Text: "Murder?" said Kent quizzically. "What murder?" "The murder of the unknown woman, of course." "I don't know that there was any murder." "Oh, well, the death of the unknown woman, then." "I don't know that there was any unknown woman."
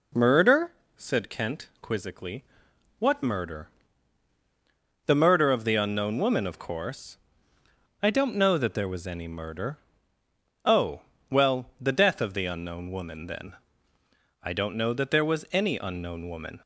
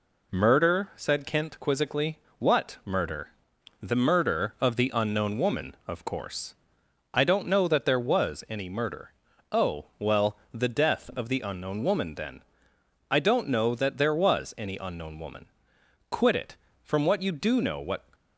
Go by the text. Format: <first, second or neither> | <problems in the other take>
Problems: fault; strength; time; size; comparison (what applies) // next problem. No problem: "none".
first | goes on to say "Quit it From what you do know what"; strong; from 16.1 s on; 1.9 s long